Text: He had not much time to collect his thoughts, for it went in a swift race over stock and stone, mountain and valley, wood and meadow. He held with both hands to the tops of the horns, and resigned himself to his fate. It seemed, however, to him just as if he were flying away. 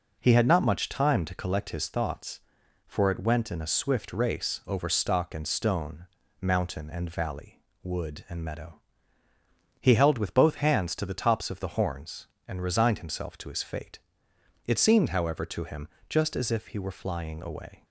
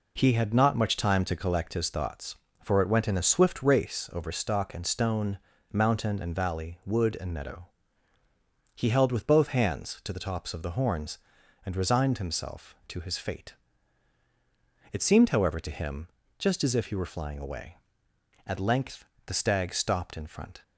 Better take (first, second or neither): first